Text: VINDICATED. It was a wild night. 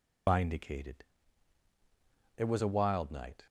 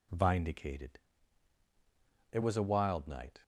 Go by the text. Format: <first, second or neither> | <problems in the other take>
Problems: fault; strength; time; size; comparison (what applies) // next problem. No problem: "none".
second | loses the start of "VINDICATED"; at 0.2 s; 110 ms